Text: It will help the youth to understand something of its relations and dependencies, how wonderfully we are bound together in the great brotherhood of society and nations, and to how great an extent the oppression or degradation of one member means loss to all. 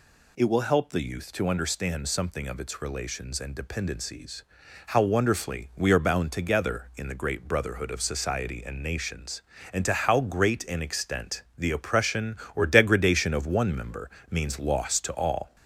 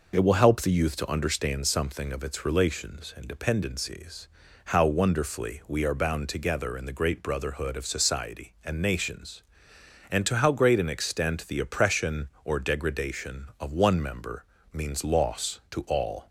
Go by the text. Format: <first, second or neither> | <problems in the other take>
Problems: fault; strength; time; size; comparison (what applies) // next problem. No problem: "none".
second | gets louder; slight; throughout; 2 dB // pauses between "member" and "means"; slight; at 14.0 s; 0.20 s long; slight in the second